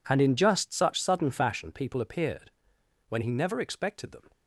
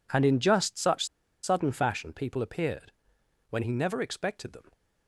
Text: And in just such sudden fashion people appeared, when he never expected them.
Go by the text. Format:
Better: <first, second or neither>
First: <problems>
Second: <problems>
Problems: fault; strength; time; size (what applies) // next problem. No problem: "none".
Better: first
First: none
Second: pauses between "such" and "sudden"; at 1.0 s; 0.37 s long